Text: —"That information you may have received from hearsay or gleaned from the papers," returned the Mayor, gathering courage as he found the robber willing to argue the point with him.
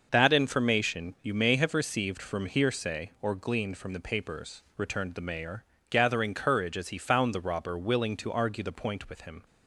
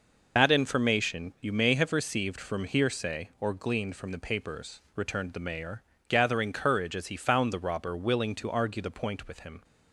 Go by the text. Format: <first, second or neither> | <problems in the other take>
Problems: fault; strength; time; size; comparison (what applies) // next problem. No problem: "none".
first | loses the start of "That"; at 0.3 s; 60 ms